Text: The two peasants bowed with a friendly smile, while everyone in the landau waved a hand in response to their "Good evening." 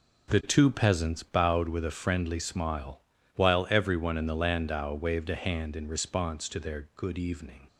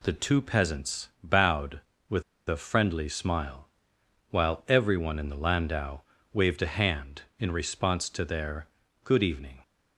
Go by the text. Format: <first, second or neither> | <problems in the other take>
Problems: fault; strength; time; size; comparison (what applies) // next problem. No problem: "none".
first | pauses between "with" and "a"; slight; at 2.2 s; 0.25 s long // pauses between "landau" and "waved"; slight; at 6.0 s; 0.32 s long // pauses between "their" and "Good"; at 8.6 s; 0.38 s long